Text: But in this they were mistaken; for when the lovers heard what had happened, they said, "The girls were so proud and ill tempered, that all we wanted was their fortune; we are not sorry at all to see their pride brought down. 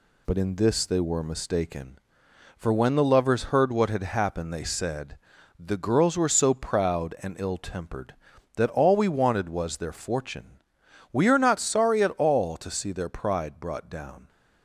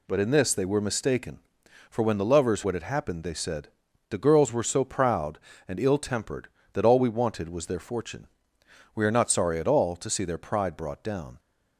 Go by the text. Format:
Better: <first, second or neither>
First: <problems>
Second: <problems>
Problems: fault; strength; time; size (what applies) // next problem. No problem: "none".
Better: first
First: none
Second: skips "heard"; at 2.6 s